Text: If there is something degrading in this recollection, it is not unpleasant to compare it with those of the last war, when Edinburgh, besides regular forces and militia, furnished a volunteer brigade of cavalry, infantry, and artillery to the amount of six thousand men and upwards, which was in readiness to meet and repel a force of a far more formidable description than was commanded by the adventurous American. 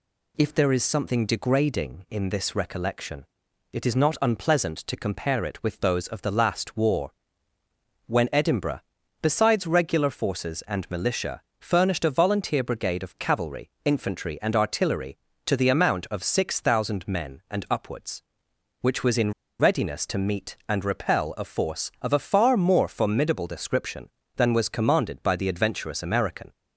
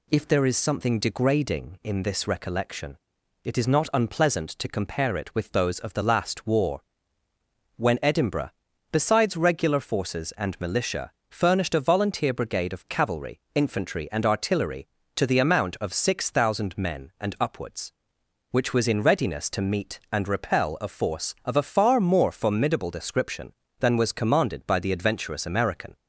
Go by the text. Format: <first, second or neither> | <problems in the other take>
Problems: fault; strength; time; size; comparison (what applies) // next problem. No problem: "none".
second | pauses between "in" and "readiness"; slight; at 19.3 s; 0.28 s long